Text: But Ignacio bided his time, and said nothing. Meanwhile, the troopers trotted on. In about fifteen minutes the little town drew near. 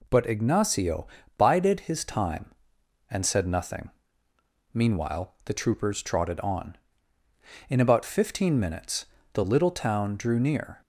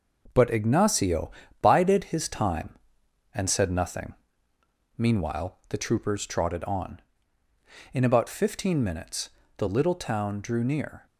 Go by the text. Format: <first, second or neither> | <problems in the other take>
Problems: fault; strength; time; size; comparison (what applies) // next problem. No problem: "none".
first | gets quieter; throughout; 6 dB // pauses between "Ignacio" and "bided"; slight; at 1.3 s; 0.30 s long; slight in the first // pauses between "minutes" and "the"; slight; at 9.3 s; 0.28 s long; slight in the first